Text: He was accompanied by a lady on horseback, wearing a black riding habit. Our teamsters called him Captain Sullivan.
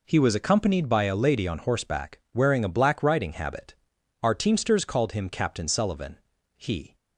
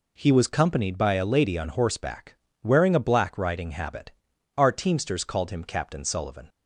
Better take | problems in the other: second | goes on to say "He"; slight; from 6.5 s on; 0.38 s long

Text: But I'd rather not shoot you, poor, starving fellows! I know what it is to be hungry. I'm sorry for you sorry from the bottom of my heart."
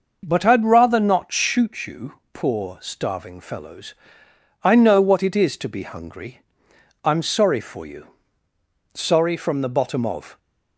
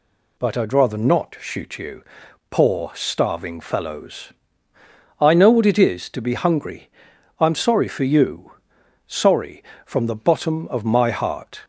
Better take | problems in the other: second | pauses between "you" and "sorry"; noticeable; at 8.0 s; 0.88 s long; noticeable in the second // stops before "my heart"; at 10.3 s

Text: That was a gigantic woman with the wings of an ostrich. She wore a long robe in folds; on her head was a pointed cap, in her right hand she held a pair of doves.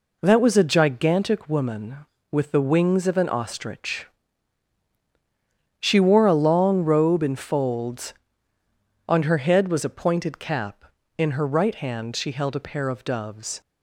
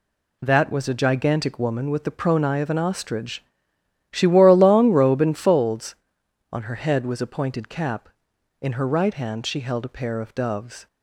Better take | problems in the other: first | says "pronai" for "wings"; at 2.1 s

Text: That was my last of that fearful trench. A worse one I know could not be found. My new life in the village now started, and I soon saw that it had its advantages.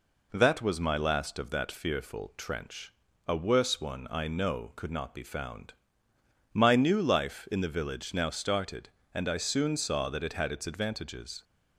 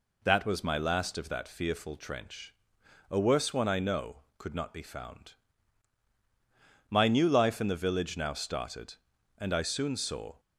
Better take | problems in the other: first | stops before "that it had its advantages"; at 10.3 s

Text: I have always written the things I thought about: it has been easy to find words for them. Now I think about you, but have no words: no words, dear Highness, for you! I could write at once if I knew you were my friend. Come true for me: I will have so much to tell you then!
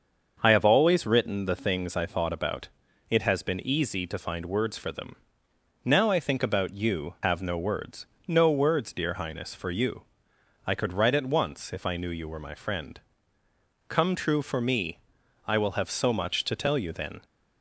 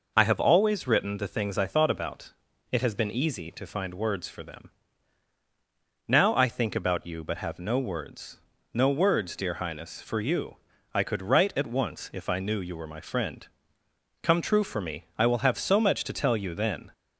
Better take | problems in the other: second | starts louder than the rest; until 1.4 s; 6.5 dB // skips "but"; at 7.1 s

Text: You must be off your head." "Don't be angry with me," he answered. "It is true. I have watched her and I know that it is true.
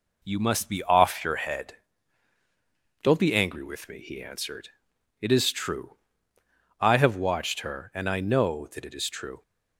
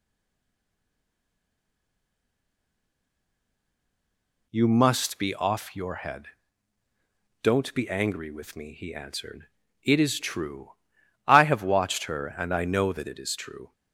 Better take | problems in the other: first | stays silent before the first word; strong; until 4.5 s; 4.5 s long

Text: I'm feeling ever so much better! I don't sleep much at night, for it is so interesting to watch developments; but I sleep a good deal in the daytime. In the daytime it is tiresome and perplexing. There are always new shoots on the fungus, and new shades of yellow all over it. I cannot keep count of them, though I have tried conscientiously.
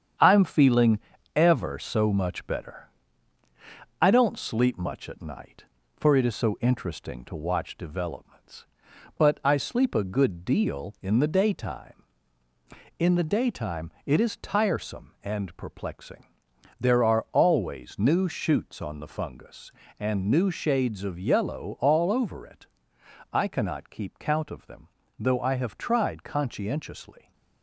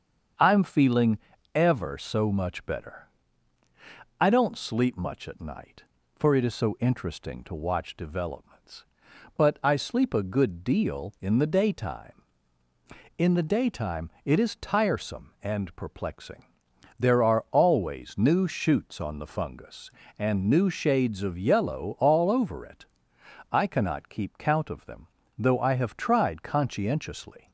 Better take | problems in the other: second | gets quieter; noticeable; throughout; 4.5 dB // starts louder than the rest; strong; until 1.5 s; 8.5 dB; strong in the second // pauses between "feeling" and "ever"; slight; at 0.9 s; 0.34 s long; slight in the second // pauses between "daytime" and "it"; slight; at 13.8 s; 0.16 s long; slight in the second

